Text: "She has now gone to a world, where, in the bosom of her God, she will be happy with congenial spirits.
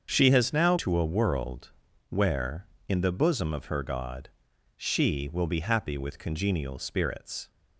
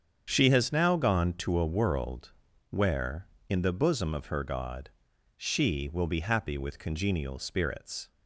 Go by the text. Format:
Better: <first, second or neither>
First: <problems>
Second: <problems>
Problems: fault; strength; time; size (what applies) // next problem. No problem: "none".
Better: second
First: starts louder than the rest; until 1.1 s; 7 dB // skips "gone"; at 0.7 s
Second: starts louder than the rest; strong; until 1.3 s; 7.5 dB